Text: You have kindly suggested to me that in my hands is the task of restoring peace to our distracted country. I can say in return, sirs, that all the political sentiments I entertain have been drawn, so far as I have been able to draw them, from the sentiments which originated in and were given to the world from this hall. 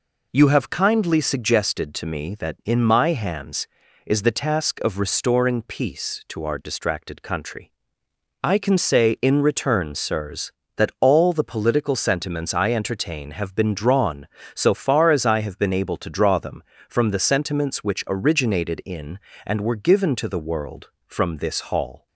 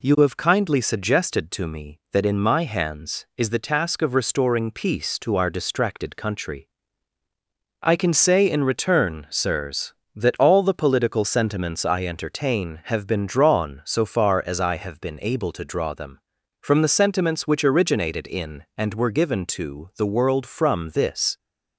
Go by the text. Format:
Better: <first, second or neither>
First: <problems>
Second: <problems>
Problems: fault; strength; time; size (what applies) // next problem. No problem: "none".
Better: first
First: none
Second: stops before "hall"; at 21.3 s